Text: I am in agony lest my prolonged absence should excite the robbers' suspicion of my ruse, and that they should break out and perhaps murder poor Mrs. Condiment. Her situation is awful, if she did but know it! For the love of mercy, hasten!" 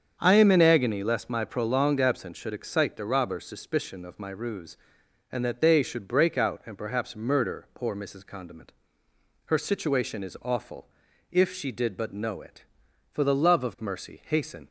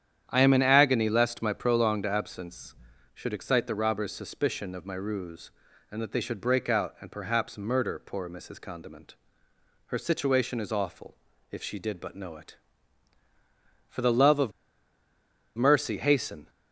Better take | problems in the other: first | starts louder than the rest; strong; until 1.2 s; 9.5 dB; strong in the first // pauses between "of" and "mercy"; at 14.5 s; 1.0 s long

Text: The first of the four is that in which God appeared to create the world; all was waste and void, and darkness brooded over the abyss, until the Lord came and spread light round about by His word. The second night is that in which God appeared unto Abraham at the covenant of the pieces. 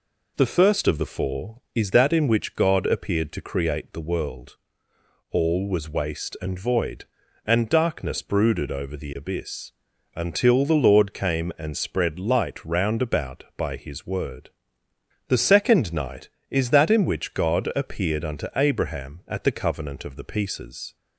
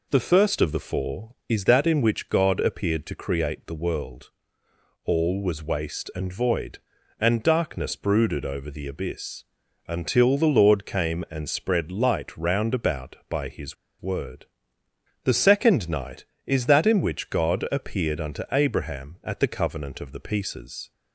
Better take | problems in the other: first | pauses between "His" and "word"; slight; at 13.7 s; 0.26 s long

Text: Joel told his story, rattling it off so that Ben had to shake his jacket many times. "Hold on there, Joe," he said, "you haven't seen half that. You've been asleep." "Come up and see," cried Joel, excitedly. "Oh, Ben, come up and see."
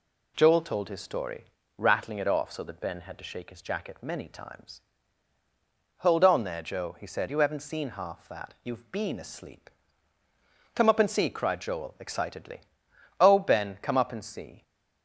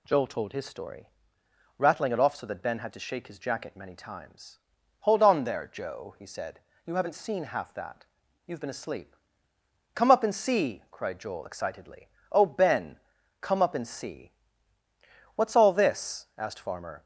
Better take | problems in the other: first | goes on to say "What's all this asked Farmer"; strong; from 15.3 s on; 1.7 s long

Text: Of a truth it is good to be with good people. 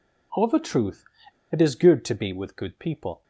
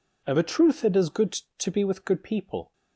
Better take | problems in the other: second | pauses between "truth" and "it"; noticeable; at 1.0 s; 0.46 s long

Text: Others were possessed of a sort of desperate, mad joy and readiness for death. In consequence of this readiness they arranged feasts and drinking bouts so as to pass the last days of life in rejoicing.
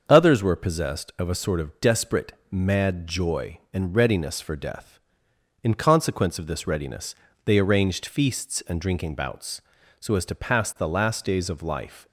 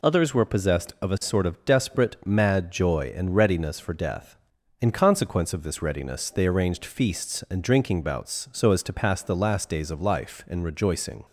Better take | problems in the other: second | starts louder than the rest; until 1.0 s; 6.5 dB // pauses between "readiness" and "they"; slight; at 7.1 s; 0.28 s long // stops before "in rejoicing"; at 12.0 s

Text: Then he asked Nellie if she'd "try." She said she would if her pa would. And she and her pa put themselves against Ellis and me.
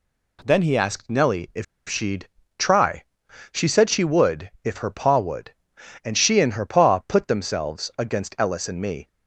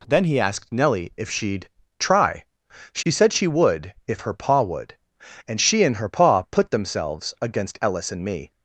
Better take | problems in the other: second | pauses between "if" and "she'd"; slight; at 1.6 s; 0.24 s long // pauses between "she'd" and "try"; slight; at 2.2 s; 0.32 s long; slight in the second

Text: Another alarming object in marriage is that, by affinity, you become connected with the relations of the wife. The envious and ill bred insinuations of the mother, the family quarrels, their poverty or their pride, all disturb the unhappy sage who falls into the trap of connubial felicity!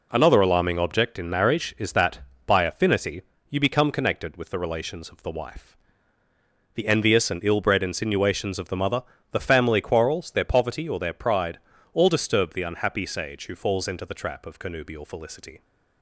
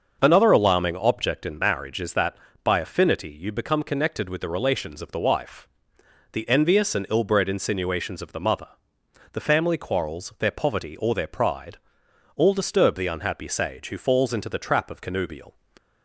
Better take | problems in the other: first | starts louder than the rest; until 1.2 s; 6.5 dB // stops before "felicity"; at 15.7 s

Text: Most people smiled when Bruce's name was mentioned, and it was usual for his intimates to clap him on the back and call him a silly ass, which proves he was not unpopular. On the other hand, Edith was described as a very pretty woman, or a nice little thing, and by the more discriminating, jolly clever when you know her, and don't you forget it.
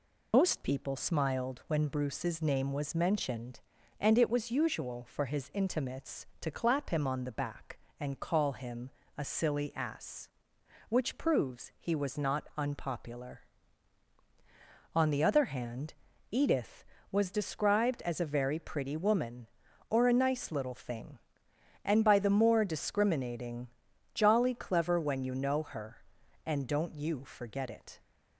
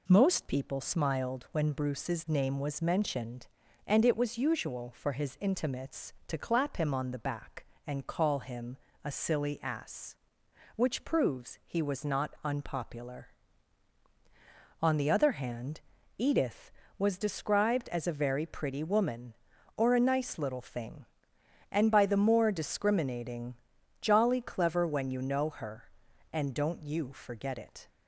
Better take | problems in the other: second | loses the start of "Most"; at 0.3 s; 120 ms // pauses between "him" and "a"; slight; at 8.8 s; 0.28 s long; slight in the second

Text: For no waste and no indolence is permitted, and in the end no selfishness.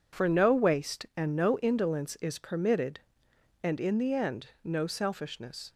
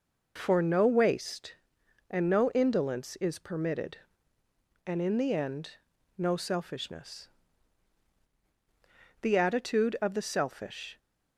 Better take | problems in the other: first | pauses between "end" and "no"; at 5.7 s; 0.38 s long // goes on to say "The attitude of the selfish"; strong; from 9.2 s on; 1.7 s long

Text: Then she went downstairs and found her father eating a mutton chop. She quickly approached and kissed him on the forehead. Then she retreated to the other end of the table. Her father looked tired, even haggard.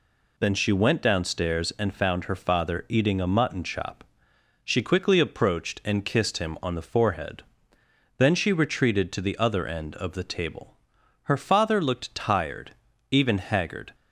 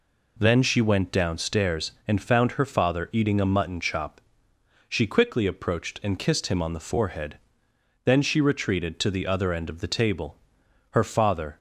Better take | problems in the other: first | stops before "looked tired even haggard"; at 11.5 s

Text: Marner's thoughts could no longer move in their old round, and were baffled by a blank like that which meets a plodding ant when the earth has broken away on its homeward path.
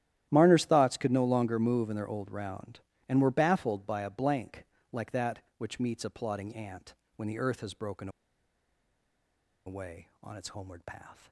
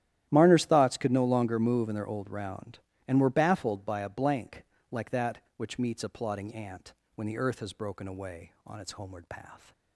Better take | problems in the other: second | starts louder than the rest; strong; until 1.3 s; 12 dB; strong in the second // pauses between "blank" and "like"; slight; at 4.6 s; 0.26 s long; slight in the second // pauses between "ant" and "when"; slight; at 6.9 s; 0.22 s long; slight in the second // pauses between "broken" and "away"; strong; at 8.0 s; 1.5 s long

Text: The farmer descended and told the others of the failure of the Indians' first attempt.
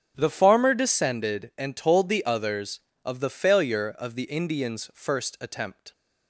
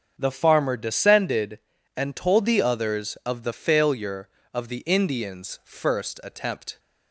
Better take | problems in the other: neither | starts louder than the rest; the same in both

